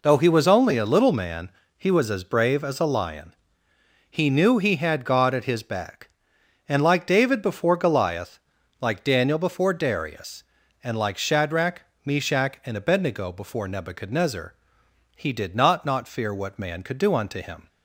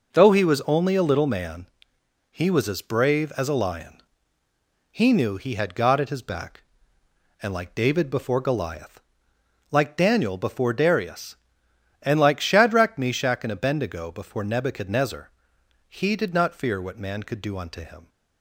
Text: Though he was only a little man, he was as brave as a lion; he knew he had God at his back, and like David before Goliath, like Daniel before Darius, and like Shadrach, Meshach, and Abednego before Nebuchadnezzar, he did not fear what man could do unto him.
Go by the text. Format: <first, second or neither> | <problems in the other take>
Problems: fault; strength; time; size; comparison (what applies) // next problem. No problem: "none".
second | says "not" twice; at 15.8 s